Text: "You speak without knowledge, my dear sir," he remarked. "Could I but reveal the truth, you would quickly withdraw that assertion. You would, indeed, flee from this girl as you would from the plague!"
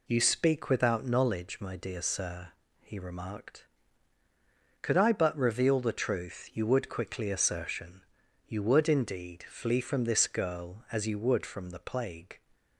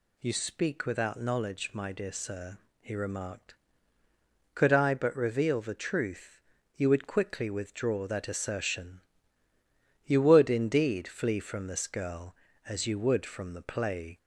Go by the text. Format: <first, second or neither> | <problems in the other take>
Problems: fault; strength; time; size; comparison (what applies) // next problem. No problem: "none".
second | skips "withdraw that"; at 7.3 s